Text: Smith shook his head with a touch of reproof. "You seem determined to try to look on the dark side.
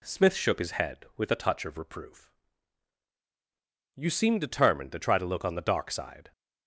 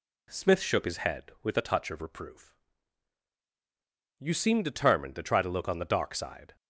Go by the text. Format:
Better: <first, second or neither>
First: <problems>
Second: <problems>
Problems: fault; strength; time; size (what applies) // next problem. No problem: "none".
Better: neither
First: none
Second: none